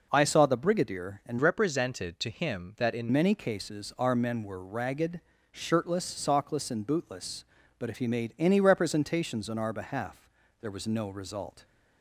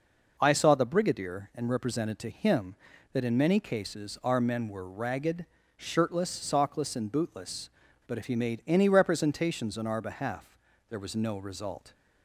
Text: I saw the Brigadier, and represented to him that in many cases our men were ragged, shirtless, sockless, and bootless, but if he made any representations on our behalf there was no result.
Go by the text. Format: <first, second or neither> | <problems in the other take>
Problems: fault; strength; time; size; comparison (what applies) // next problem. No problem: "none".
second | changes voice from "represented" to "in"; from 1.3 to 3.0 s; 1.7 s long // pauses between "behalf" and "there"; slight; at 10.2 s; 0.32 s long; slight in the second